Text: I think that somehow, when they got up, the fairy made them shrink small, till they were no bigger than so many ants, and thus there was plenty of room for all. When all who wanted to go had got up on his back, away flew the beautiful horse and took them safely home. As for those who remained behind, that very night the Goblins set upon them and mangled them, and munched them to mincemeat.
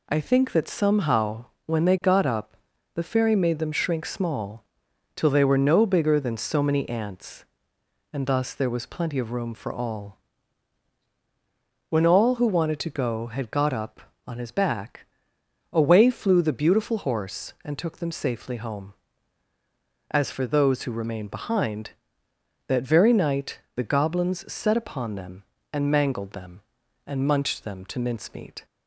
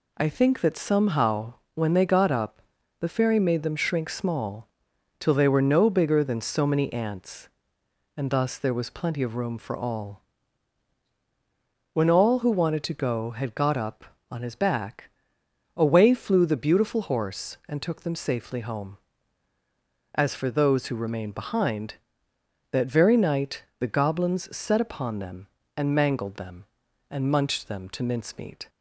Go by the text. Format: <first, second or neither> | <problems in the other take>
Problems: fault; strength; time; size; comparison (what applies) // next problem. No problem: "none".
neither | pauses between "night" and "the"; slight; the same in both